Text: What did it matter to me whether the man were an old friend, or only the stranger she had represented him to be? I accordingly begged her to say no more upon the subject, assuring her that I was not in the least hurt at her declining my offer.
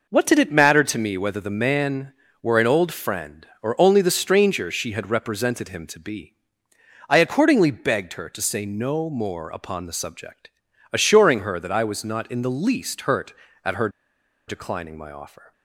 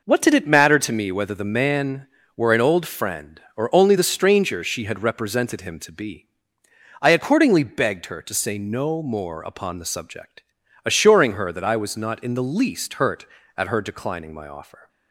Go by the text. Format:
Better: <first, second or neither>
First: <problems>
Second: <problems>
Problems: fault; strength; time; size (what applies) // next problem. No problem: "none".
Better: second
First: pauses between "her" and "declining"; noticeable; at 13.8 s; 0.58 s long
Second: none